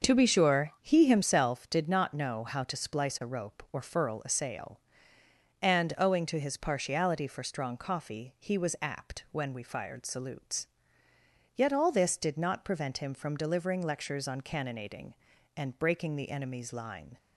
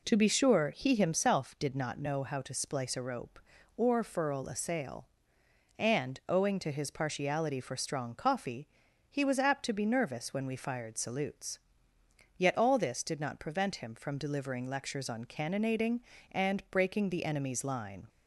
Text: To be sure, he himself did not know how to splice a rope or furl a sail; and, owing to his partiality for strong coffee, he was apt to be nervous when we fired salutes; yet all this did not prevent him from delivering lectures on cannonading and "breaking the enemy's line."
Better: second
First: starts louder than the rest; until 1.1 s; 6.5 dB // skips "to be nervous"; at 9.2 s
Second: none

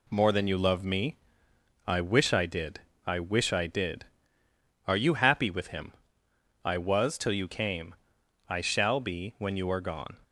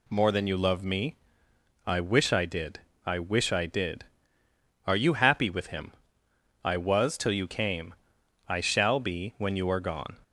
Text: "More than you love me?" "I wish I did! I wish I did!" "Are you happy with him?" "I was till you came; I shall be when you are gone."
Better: second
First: gets quieter; throughout; 4 dB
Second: none

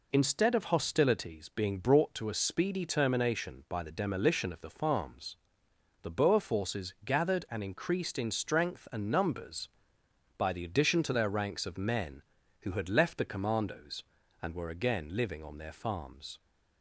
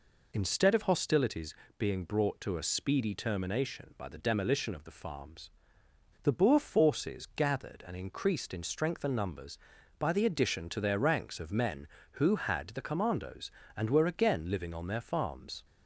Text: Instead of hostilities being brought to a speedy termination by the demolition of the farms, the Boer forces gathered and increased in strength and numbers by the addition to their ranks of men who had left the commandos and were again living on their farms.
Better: first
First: none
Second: pauses between "hostilities" and "being"; slight; at 1.5 s; 0.24 s long // skips "left"; at 12.6 s

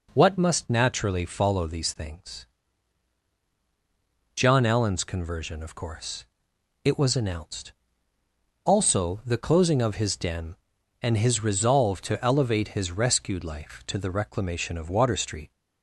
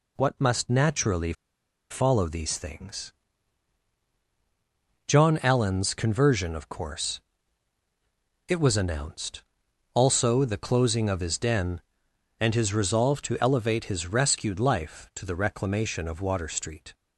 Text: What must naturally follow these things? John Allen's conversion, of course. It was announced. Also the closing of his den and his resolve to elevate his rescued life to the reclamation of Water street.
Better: first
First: none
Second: pauses between "naturally" and "follow"; noticeable; at 1.3 s; 0.59 s long

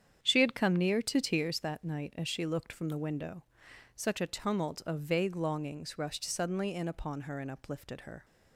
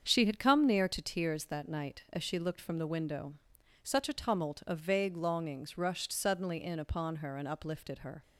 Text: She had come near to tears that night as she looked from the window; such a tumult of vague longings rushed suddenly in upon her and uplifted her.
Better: neither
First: starts louder than the rest; strong; until 1.2 s; 8.5 dB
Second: starts louder than the rest; strong; until 1.1 s; 7 dB

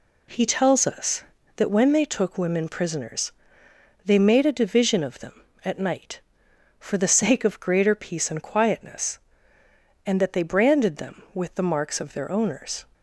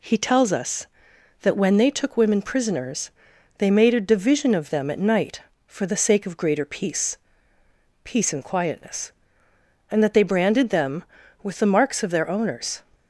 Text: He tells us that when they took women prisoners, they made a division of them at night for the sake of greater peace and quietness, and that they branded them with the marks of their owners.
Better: first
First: none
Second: says "peace" twice; at 8.0 s

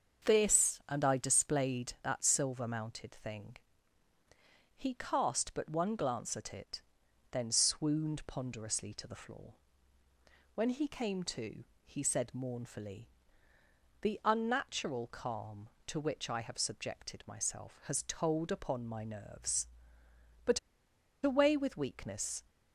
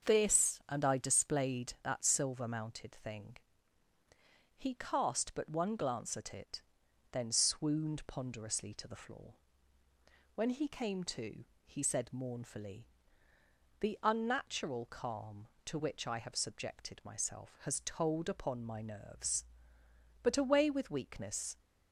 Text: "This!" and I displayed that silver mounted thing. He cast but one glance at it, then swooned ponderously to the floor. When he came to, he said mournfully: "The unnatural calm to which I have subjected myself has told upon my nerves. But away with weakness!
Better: second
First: starts louder than the rest; until 1.3 s; 6.5 dB // pauses between "But" and "away"; noticeable; at 20.5 s; 0.65 s long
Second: starts louder than the rest; until 1.1 s; 6.5 dB

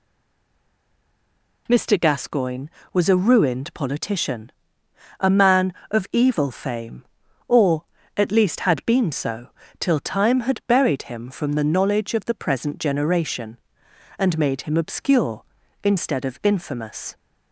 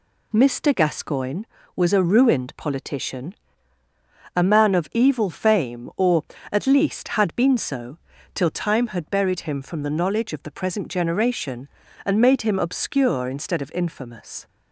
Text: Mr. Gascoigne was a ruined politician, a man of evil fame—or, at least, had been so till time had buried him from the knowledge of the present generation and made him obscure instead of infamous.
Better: second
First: stays silent before the first word; noticeable; until 1.6 s; 1.6 s long // pauses between "so" and "till"; slight; at 9.4 s; 0.32 s long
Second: pauses between "so" and "till"; slight; at 7.9 s; 0.36 s long

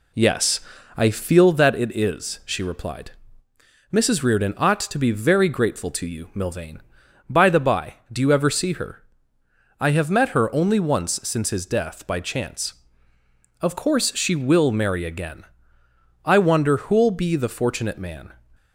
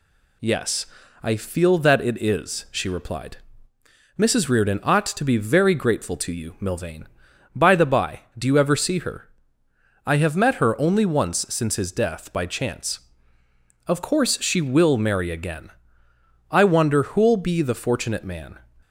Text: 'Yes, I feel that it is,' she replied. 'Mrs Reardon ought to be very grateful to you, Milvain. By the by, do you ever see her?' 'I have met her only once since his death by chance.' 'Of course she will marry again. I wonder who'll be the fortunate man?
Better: second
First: starts louder than the rest; slight; until 1.6 s; 2 dB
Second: none

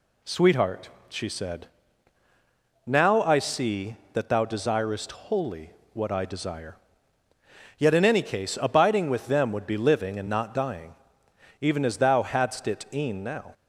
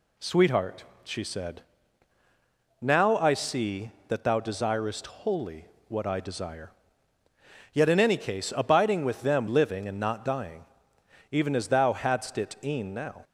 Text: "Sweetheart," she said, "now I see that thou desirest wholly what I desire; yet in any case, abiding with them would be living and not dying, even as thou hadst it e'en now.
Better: first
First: pauses between "wholly" and "what"; slight; at 5.7 s; 0.24 s long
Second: pauses between "wholly" and "what"; slight; at 5.6 s; 0.24 s long // skips "would be"; at 9.4 s

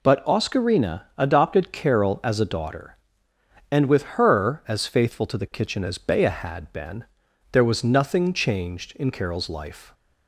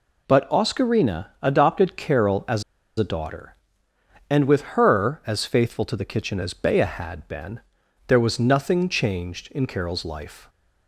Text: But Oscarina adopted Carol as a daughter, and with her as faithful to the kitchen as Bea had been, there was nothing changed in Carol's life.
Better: first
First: none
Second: pauses between "as" and "a"; slight; at 2.6 s; 0.36 s long

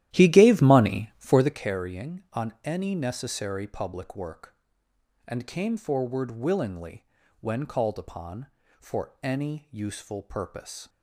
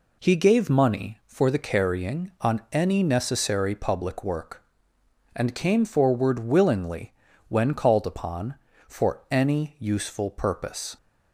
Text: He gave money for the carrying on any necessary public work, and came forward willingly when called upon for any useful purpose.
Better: second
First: starts louder than the rest; strong; until 1.7 s; 13 dB // pauses between "willingly" and "when"; slight; at 7.0 s; 0.34 s long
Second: pauses between "willingly" and "when"; slight; at 7.1 s; 0.34 s long

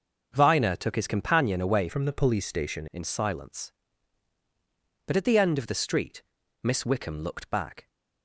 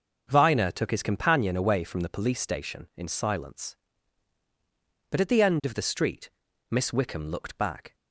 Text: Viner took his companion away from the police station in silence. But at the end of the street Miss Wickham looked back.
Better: second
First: starts louder than the rest; noticeable; until 1.3 s; 6 dB // changes voice from "from" to "station"; from 1.8 to 2.8 s; 1.0 s long // pauses between "street" and "Miss"; at 6.2 s; 0.42 s long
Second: starts louder than the rest; until 1.3 s; 6 dB // pauses between "street" and "Miss"; at 6.2 s; 0.42 s long

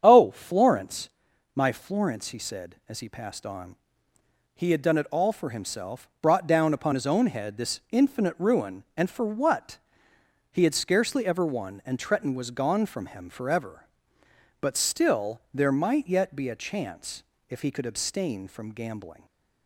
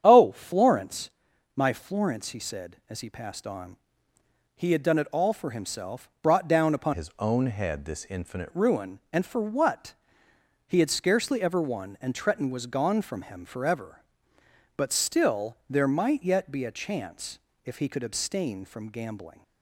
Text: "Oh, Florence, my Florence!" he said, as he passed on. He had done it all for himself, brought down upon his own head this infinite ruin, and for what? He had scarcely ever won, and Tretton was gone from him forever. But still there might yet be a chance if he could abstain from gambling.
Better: first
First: starts louder than the rest; strong; until 1.0 s; 8 dB // pauses between "chance" and "if"; slight; at 17.2 s; 0.26 s long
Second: starts louder than the rest; strong; until 1.0 s; 8.5 dB // changes voice from "his" to "infinite"; from 6.9 to 8.4 s; 1.5 s long // pauses between "chance" and "if"; slight; at 17.3 s; 0.26 s long

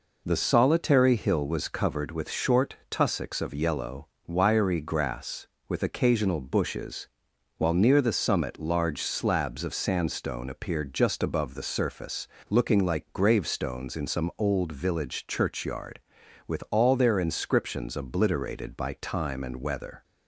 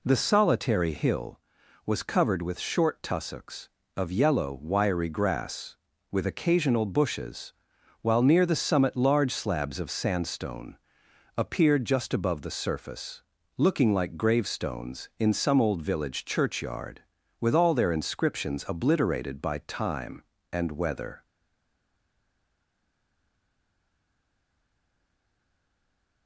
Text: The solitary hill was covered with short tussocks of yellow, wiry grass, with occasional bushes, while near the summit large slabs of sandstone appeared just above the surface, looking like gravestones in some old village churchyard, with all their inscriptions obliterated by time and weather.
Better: first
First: none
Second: pauses between "sandstone" and "appeared"; noticeable; at 10.7 s; 0.62 s long // stays silent after the last word; strong; from 21.2 s on; 5.0 s long

